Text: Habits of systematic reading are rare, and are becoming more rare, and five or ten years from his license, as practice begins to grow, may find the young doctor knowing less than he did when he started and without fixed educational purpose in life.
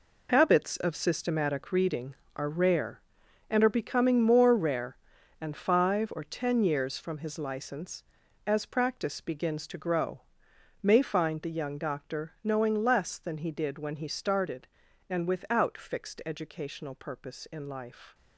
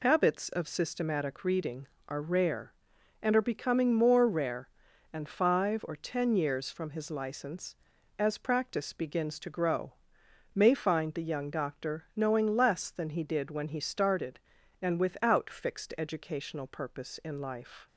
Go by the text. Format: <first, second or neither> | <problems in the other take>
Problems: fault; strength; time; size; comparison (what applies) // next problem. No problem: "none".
second | gets quieter; strong; throughout; 10.5 dB